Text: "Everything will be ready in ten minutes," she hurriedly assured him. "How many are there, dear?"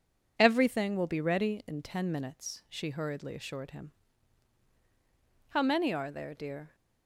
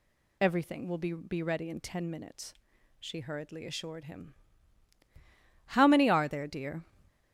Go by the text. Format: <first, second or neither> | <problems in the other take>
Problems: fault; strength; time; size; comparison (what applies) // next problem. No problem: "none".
first | says "be" twice; at 1.1 s